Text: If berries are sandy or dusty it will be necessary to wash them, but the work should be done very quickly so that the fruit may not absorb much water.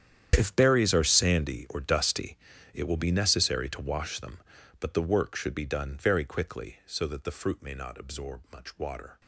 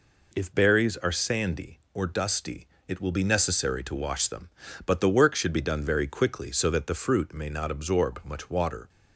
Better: second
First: gets quieter; strong; throughout; 16.5 dB // pauses between "dusty" and "it"; slight; at 2.3 s; 0.36 s long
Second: pauses between "dusty" and "it"; slight; at 2.6 s; 0.22 s long

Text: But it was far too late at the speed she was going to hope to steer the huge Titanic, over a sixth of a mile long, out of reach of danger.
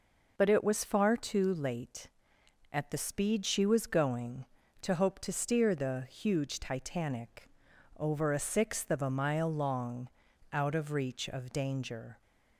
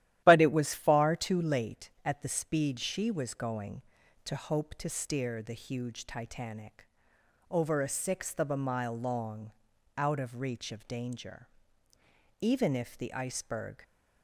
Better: first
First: none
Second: starts louder than the rest; strong; until 1.2 s; 13 dB // goes on to say "Even if the iceberg"; from 12.4 s on; 1.4 s long

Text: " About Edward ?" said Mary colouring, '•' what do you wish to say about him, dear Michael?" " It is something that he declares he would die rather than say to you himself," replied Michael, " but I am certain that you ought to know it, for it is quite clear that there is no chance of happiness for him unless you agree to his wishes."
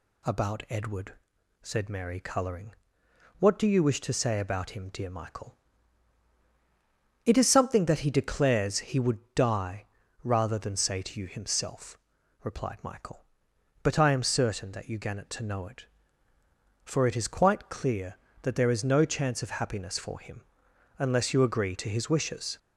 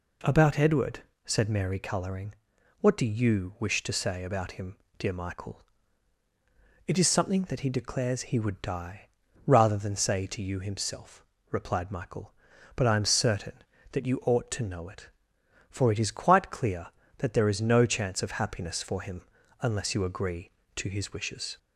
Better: second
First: pauses between "die" and "rather"; at 9.8 s; 0.38 s long // says "gannet" for "ought"; at 14.9 s // pauses between "him" and "unless"; noticeable; at 20.4 s; 0.56 s long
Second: pauses between "die" and "rather"; at 9.0 s; 0.40 s long // pauses between "him" and "unless"; at 19.2 s; 0.38 s long

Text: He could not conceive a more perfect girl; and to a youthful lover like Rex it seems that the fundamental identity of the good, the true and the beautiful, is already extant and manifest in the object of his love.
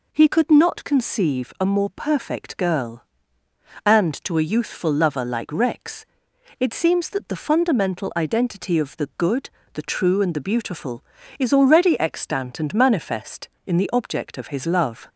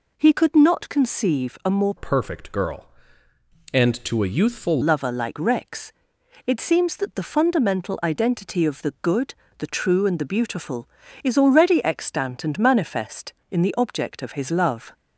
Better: first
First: pauses between "Rex" and "it"; noticeable; at 6.0 s; 0.54 s long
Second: changes voice from "perfect" to "youthful"; from 1.9 to 4.8 s; 2.9 s long // pauses between "Rex" and "it"; noticeable; at 5.9 s; 0.54 s long

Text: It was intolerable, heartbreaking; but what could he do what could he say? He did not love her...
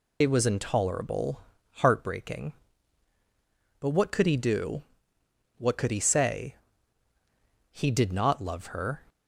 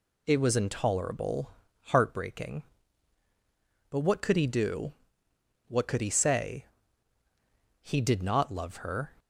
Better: second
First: loses the start of "It"; at 0.2 s; 40 ms // pauses between "do" and "what"; noticeable; at 4.8 s; 0.74 s long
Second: pauses between "do" and "what"; noticeable; at 4.9 s; 0.74 s long

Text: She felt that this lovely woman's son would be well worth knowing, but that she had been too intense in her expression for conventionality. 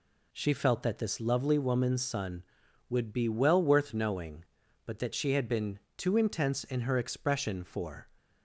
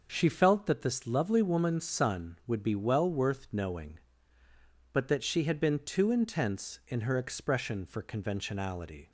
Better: second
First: pauses between "been" and "too"; slight; at 5.7 s; 0.18 s long // stops before "conventionality"; at 8.1 s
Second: none

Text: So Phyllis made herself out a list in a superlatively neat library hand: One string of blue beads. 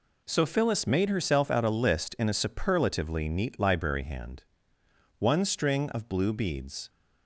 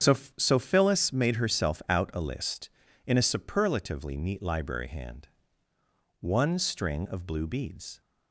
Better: first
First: none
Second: starts louder than the rest; strong; until 1.2 s; 9 dB // says "So" twice; at 0.3 s

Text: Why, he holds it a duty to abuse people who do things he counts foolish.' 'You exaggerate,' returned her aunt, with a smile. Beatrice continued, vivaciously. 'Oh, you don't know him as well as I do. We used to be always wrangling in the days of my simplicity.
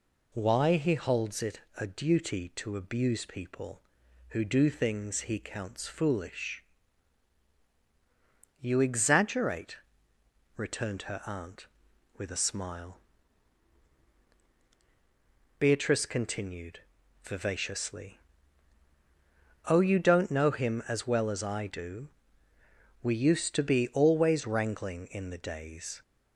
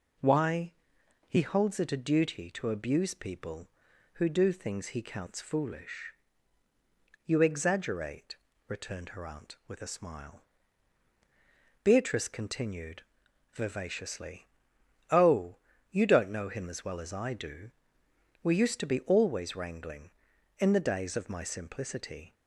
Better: second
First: pauses between "it" and "a"; slight; at 1.6 s; 0.16 s long // stops before "of my simplicity"; at 26.0 s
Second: none

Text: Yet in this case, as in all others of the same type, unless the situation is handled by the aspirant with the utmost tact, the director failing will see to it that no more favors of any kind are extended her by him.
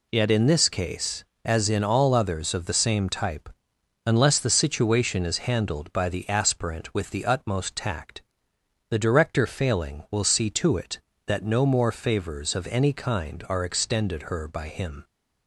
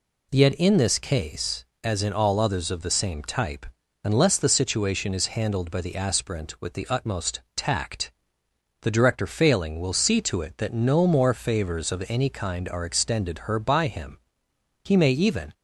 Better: first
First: none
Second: goes on to say "He may even"; noticeable; from 14.8 s on; 0.68 s long

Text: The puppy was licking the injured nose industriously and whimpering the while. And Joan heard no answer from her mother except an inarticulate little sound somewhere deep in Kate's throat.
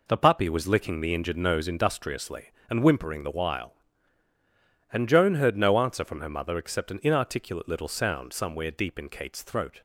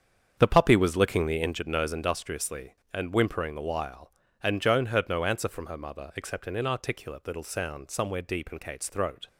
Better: first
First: none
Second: starts louder than the rest; strong; until 1.5 s; 7.5 dB

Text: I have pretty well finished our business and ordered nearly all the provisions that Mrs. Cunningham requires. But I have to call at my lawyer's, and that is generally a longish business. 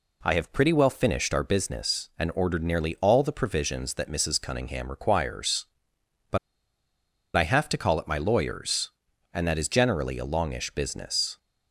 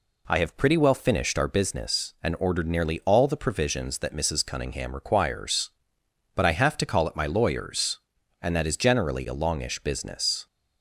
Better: second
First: pauses between "But" and "I"; noticeable; at 6.3 s; 0.97 s long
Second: none

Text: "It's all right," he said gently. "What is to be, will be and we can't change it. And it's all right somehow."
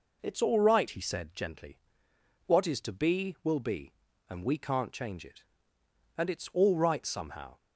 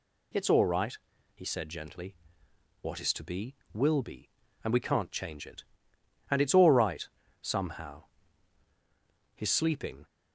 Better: first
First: none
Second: pauses between "right" and "somehow"; slight; at 7.0 s; 0.36 s long // goes on to say "His sleeping"; noticeable; from 9.3 s on; 0.70 s long

